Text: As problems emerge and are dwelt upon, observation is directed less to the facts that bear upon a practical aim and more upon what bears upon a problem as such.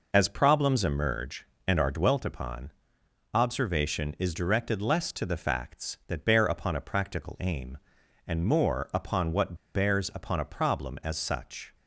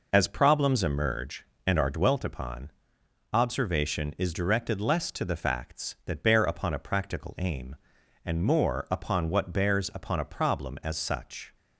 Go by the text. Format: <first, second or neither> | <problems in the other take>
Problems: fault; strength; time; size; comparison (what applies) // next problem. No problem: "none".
second | pauses between "what" and "bears"; slight; at 9.5 s; 0.20 s long